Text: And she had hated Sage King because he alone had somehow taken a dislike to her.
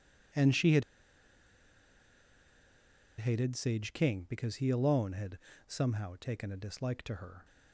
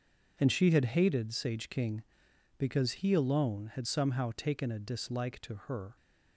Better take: second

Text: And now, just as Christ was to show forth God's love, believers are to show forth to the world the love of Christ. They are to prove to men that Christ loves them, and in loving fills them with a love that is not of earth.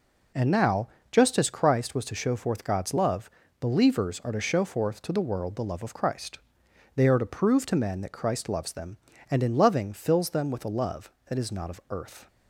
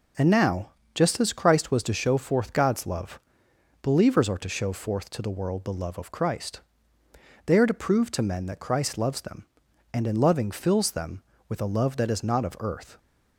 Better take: neither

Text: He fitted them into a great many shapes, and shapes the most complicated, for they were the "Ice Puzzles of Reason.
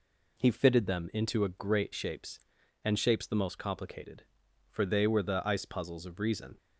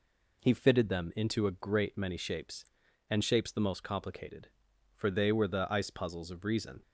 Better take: second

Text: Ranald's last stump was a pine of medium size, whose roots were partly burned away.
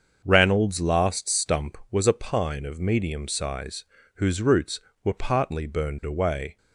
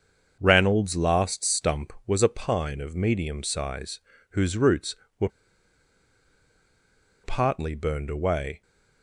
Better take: first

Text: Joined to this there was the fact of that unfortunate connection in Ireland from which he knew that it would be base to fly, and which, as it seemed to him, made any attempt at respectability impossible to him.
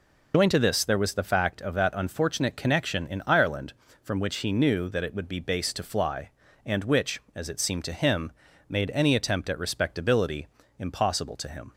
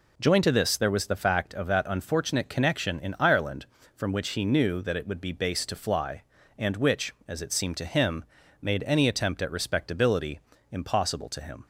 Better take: second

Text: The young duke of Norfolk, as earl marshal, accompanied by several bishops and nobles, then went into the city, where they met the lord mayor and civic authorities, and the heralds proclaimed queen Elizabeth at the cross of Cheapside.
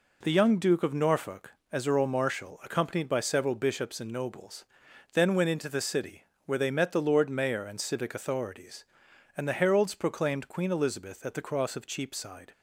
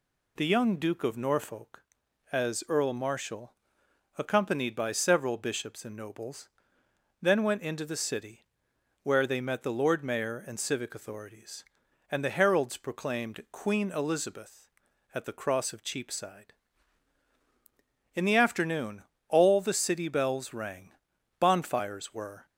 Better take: first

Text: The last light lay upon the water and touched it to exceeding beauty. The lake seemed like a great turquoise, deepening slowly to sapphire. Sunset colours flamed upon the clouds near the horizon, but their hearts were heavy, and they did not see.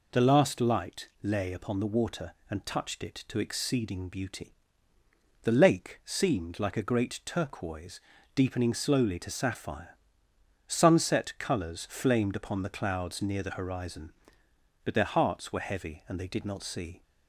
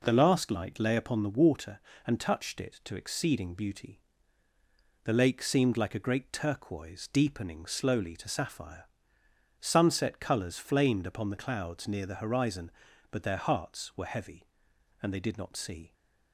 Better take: neither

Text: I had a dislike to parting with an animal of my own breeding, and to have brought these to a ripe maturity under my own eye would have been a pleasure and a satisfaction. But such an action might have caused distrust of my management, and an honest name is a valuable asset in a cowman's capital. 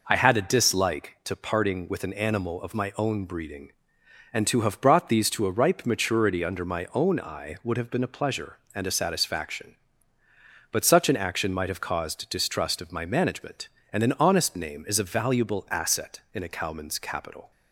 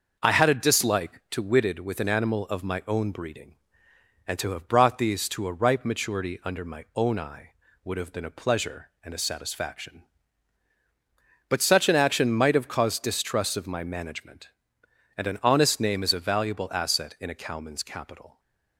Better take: first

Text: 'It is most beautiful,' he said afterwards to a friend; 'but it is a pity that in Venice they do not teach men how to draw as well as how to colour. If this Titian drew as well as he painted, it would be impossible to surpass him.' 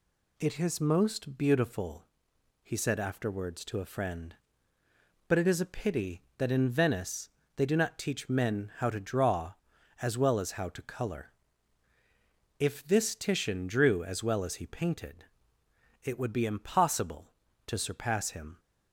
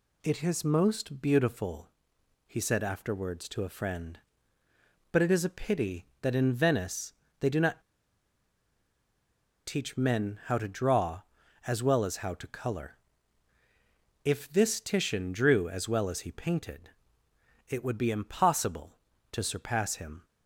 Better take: first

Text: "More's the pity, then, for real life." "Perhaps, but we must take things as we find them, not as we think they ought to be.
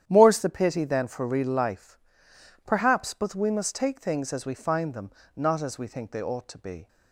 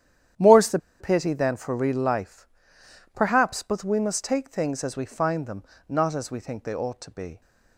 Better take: first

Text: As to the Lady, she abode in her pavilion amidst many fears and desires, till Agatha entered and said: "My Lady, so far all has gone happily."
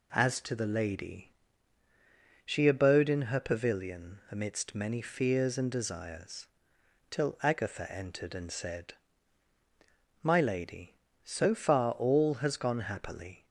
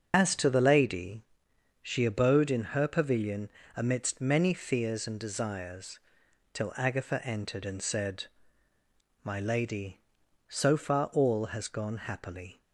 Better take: first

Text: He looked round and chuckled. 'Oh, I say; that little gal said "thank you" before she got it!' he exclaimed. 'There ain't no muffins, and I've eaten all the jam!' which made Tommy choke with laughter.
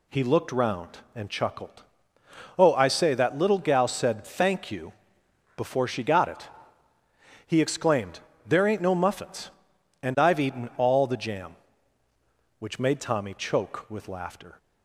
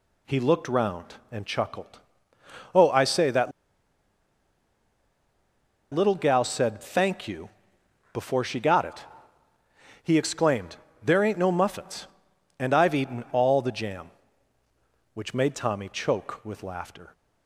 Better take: first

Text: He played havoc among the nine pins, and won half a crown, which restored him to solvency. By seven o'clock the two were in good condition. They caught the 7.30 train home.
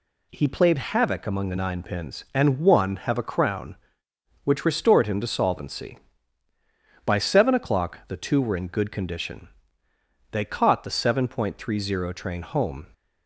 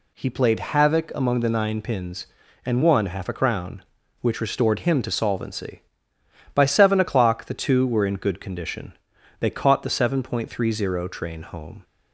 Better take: second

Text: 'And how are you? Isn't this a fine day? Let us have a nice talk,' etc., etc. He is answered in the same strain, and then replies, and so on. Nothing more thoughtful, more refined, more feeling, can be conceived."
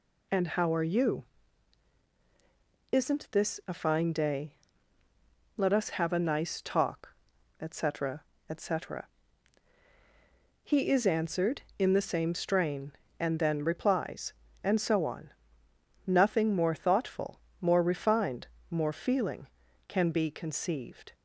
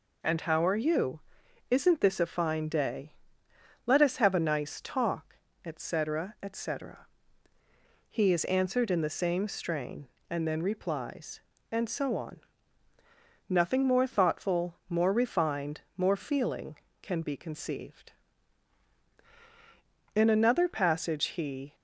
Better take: first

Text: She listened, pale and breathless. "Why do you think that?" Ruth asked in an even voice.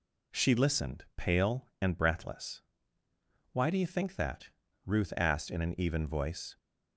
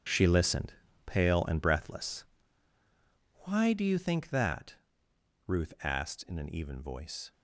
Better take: first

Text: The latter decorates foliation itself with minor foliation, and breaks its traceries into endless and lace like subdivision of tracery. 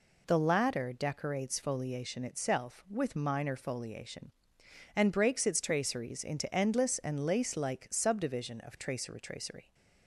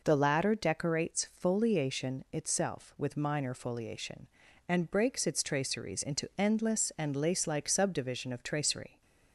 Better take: second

